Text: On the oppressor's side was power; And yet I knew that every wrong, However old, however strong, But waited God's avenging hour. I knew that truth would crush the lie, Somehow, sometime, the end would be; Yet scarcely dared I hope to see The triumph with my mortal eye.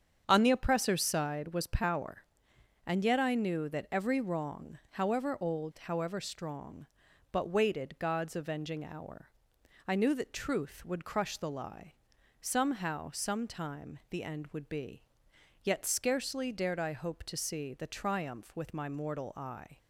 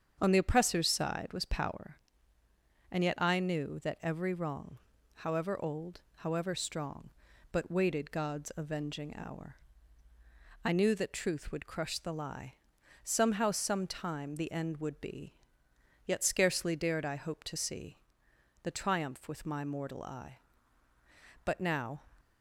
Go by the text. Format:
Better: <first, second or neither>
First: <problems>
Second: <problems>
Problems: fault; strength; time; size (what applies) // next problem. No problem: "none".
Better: first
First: starts louder than the rest; strong; until 1.2 s; 7.5 dB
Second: starts louder than the rest; strong; until 1.2 s; 7.5 dB // pauses between "see" and "The"; noticeable; at 17.9 s; 0.66 s long // goes on to say "But now"; from 21.4 s on; 0.56 s long